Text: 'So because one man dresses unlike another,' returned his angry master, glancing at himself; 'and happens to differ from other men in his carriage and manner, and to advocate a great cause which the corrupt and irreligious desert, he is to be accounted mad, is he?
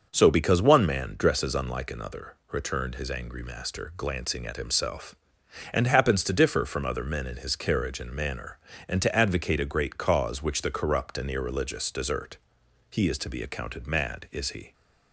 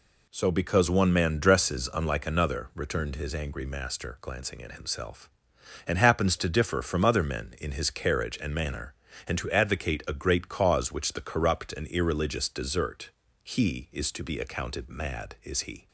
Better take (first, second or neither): neither